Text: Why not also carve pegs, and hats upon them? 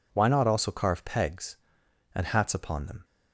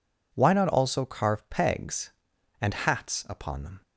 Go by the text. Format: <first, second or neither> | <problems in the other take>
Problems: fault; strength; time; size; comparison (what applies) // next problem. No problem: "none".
neither | none